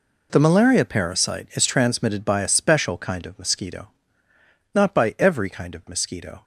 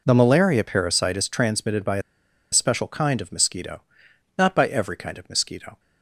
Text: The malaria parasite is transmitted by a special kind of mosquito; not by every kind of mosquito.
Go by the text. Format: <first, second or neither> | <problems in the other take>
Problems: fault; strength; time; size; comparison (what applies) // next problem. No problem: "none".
first | pauses between "a" and "special"; noticeable; at 2.0 s; 0.51 s long